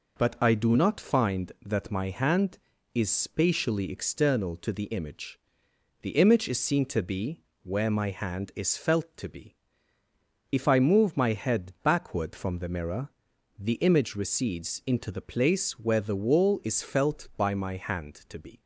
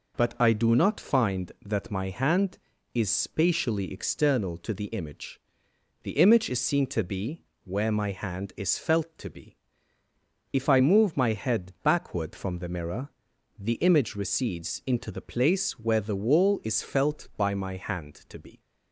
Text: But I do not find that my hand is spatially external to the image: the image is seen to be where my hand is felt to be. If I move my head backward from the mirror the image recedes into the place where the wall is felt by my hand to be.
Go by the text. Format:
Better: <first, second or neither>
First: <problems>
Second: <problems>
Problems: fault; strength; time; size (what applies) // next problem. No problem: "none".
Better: neither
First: pauses between "be" and "where"; slight; at 7.3 s; 0.24 s long // pauses between "mirror" and "the"; noticeable; at 13.0 s; 0.48 s long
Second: pauses between "be" and "where"; slight; at 7.4 s; 0.24 s long // pauses between "mirror" and "the"; noticeable; at 13.0 s; 0.48 s long